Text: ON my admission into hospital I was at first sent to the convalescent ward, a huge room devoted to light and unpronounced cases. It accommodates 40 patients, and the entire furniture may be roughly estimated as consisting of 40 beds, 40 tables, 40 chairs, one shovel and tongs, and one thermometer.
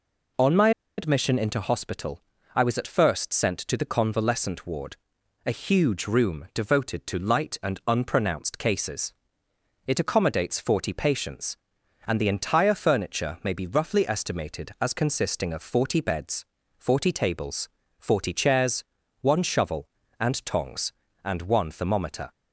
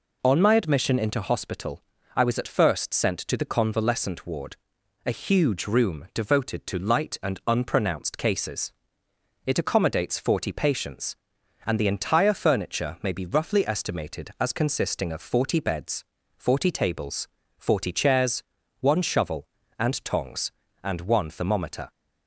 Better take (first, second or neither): second